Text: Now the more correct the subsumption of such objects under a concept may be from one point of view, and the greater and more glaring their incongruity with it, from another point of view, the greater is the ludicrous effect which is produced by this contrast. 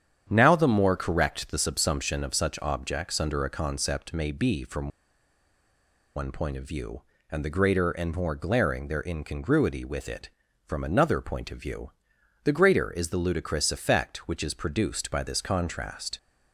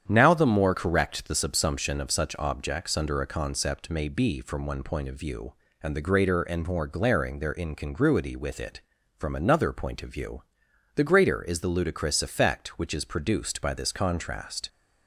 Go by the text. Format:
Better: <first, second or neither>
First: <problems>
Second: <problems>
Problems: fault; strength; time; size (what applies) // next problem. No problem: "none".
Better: second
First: starts louder than the rest; strong; until 1.3 s; 9 dB // pauses between "from" and "one"; strong; at 4.8 s; 1.2 s long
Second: starts louder than the rest; strong; until 1.1 s; 9 dB